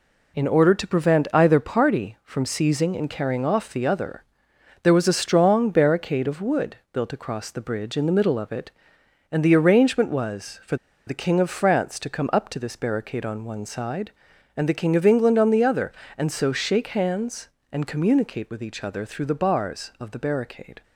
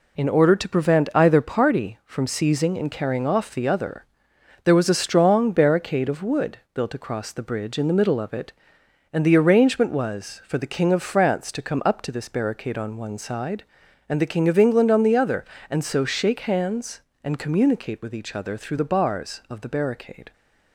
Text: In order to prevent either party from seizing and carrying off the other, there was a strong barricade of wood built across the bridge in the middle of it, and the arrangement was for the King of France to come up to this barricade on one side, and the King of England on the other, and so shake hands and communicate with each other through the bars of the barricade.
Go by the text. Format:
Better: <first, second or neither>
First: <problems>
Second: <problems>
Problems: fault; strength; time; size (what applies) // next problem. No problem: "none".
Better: second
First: pauses between "for" and "the"; slight; at 10.7 s; 0.31 s long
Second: none